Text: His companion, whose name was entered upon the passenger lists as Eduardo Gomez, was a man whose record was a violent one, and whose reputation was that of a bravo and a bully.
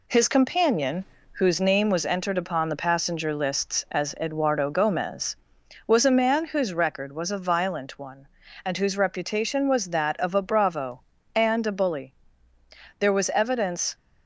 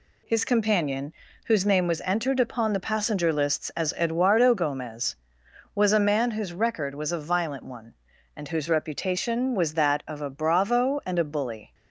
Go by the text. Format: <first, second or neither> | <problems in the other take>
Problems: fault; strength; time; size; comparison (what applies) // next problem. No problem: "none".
second | goes on to say "There was evidence"; noticeable; from 12.9 s on; 0.96 s long